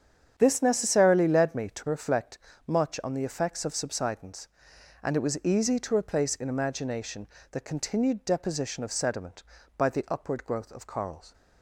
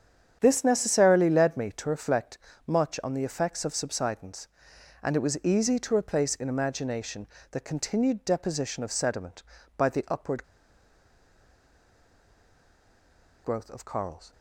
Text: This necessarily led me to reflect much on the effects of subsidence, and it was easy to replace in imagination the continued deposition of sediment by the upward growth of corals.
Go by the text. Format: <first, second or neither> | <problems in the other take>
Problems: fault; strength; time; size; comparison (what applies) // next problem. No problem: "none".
first | starts louder than the rest; strong; until 1.4 s; 8 dB; strong in the first // pauses between "reflect" and "much"; slight; at 2.3 s; 0.30 s long; slight in the first // pauses between "imagination" and "the"; slight; at 7.2 s; 0.26 s long; slight in the first // pauses between "upward" and "growth"; strong; at 10.4 s; 2.9 s long